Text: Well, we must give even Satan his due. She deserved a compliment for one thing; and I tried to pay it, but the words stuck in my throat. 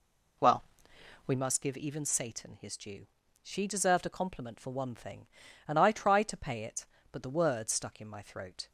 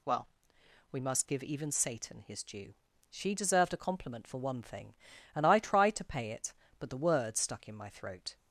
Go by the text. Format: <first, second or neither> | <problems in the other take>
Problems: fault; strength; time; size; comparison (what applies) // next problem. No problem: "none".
second | starts louder than the rest; slight; until 1.4 s; 2.5 dB